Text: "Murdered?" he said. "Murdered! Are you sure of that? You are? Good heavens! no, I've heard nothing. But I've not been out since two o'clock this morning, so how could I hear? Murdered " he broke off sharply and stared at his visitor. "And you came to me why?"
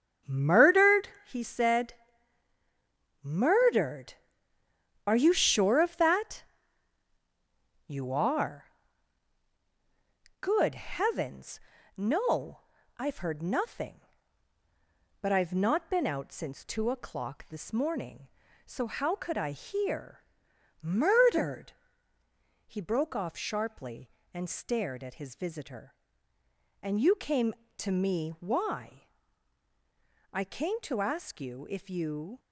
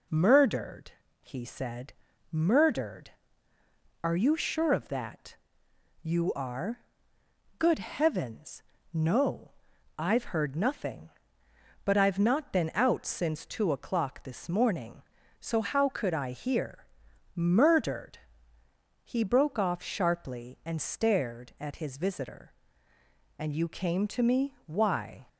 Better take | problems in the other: second | starts louder than the rest; strong; until 1.4 s; 8 dB // goes on to say "I came to ask you if you"; strong; from 30.3 s on; 2.0 s long

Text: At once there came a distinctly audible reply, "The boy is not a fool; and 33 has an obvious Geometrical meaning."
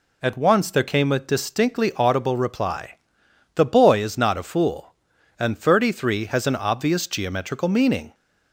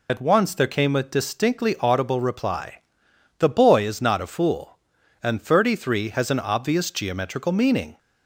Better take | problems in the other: first | loses the start of "At"; at 0.0 s; 40 ms

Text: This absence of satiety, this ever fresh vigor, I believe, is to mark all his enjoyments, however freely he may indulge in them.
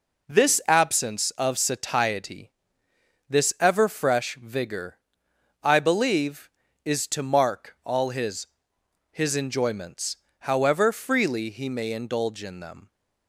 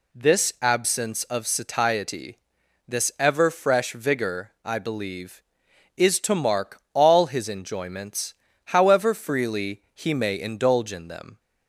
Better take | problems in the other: second | says "his" twice; at 9.1 s

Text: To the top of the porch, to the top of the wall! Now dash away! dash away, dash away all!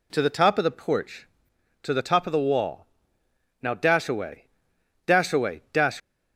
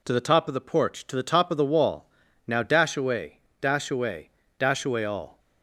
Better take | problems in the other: second | stops before "away all"; at 6.0 s

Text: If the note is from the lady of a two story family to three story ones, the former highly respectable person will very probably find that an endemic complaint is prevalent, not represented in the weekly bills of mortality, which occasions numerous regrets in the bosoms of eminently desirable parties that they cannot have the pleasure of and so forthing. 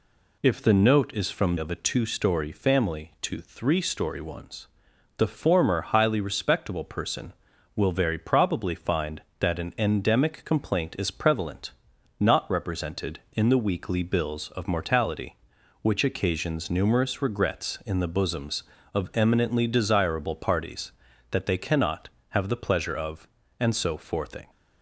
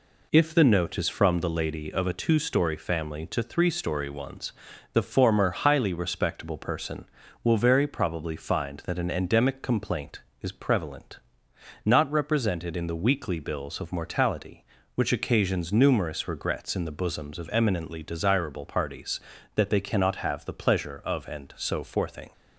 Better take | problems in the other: second | skips "the lady"; at 1.5 s

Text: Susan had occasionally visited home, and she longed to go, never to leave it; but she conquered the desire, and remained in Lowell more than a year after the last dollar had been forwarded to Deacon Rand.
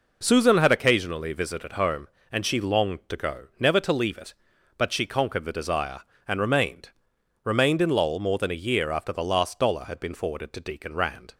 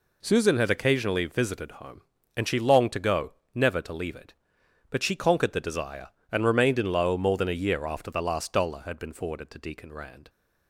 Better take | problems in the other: second | says "remained" twice; at 7.4 s

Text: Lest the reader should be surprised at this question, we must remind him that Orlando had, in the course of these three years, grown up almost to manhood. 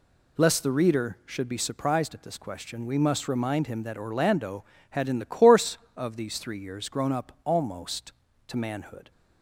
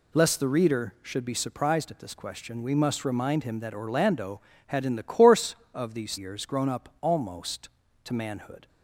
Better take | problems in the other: first | skips "three"; at 6.1 s

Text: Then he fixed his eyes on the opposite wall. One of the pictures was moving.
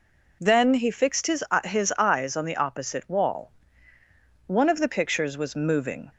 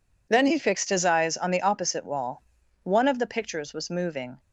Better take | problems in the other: second | says "his" twice; at 1.6 s

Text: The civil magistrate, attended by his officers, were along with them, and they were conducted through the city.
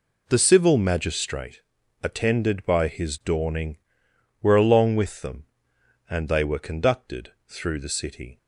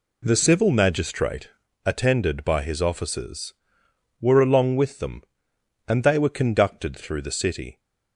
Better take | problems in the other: second | says "dawning" for "officers"; at 3.2 s // pauses between "conducted" and "through"; slight; at 7.3 s; 0.16 s long

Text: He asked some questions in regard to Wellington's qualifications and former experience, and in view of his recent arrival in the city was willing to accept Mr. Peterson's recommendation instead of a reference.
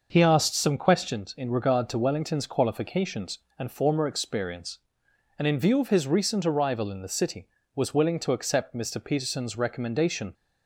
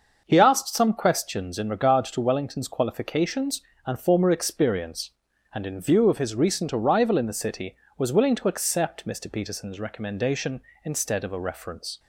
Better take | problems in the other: second | starts louder than the rest; noticeable; until 1.1 s; 6 dB; also in the second // stops before "instead of a reference"; at 10.3 s

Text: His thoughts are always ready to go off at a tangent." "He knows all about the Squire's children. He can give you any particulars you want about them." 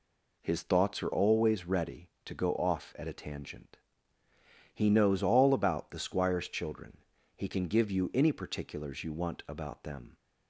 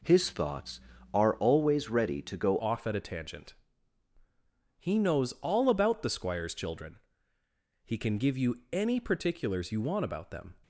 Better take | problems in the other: first | changes voice at "off"; from 2.5 s on; 8.0 s long

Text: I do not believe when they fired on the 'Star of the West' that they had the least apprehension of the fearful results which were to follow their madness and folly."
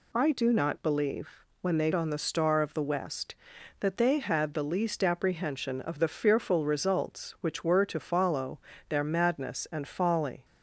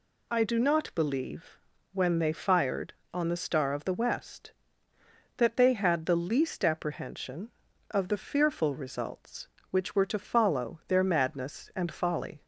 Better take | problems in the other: second | pauses between "believe" and "when"; slight; at 1.2 s; 0.32 s long; slight in the second // skips "fired"; at 1.9 s // pauses between "follow" and "their"; slight; at 8.6 s; 0.26 s long

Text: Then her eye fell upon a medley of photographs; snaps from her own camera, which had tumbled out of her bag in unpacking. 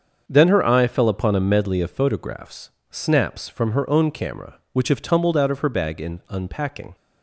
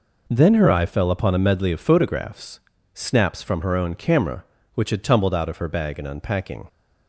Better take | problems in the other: second | starts louder than the rest; until 1.2 s; 7 dB // says "have" for "had"; at 4.8 s

